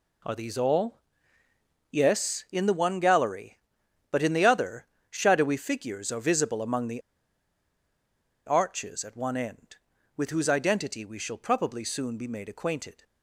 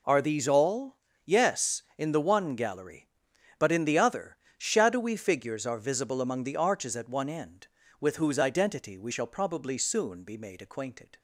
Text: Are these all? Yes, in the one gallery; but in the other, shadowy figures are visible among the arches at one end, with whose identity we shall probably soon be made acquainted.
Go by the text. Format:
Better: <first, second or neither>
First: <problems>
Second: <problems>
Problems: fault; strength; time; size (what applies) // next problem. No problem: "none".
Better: second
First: pauses between "the" and "arches"; strong; at 7.0 s; 1.4 s long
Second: none